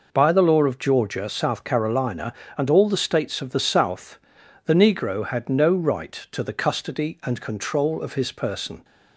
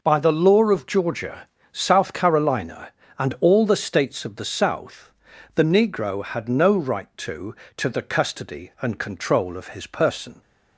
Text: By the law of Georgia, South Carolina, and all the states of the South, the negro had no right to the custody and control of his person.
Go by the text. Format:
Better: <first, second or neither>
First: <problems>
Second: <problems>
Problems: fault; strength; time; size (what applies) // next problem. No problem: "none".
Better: first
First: none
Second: says "to" twice; at 7.7 s